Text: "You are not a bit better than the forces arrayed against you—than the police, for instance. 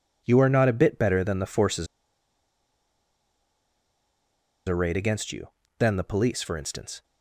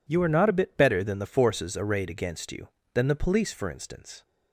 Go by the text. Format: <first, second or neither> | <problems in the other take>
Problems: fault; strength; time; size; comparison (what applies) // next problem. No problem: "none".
second | pauses between "forces" and "arrayed"; strong; at 1.8 s; 2.8 s long